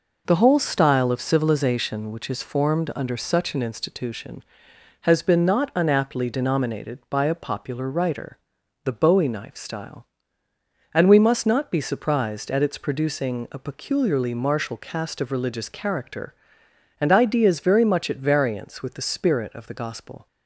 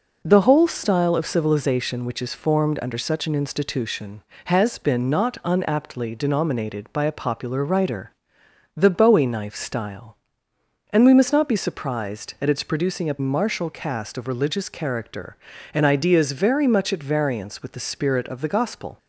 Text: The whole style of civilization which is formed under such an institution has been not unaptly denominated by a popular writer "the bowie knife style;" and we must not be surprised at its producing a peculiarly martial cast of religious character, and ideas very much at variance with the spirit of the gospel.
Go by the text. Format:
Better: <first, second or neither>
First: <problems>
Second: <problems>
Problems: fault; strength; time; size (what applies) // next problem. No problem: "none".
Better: first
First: pauses between "writer" and "the"; noticeable; at 8.3 s; 0.46 s long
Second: pauses between "writer" and "the"; noticeable; at 8.1 s; 0.62 s long // skips "peculiarly"; at 13.1 s